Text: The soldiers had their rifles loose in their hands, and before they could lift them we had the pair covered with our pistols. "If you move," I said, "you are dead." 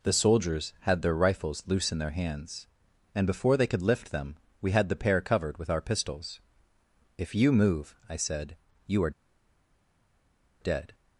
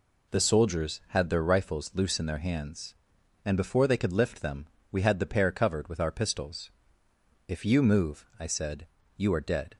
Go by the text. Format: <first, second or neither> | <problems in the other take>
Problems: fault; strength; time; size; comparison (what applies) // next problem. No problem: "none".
second | pauses between "them" and "we"; slight; at 4.3 s; 0.26 s long; slight in the second // pauses between "are" and "dead"; strong; at 9.1 s; 1.5 s long